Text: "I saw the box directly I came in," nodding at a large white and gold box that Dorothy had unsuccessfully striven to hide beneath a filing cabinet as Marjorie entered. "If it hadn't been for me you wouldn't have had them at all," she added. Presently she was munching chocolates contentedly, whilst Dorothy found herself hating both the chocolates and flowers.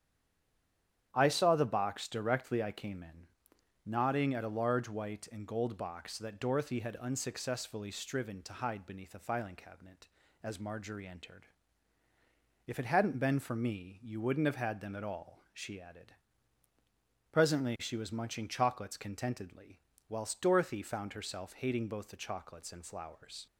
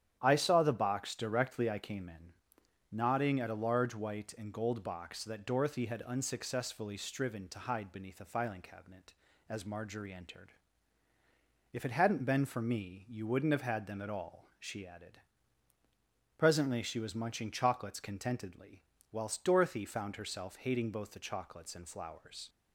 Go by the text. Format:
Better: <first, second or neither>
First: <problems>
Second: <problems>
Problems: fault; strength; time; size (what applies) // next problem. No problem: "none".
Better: second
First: stays silent before the first word; until 1.1 s; 1.1 s long // starts louder than the rest; strong; until 2.1 s; 10 dB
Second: starts louder than the rest; strong; until 1.2 s; 10 dB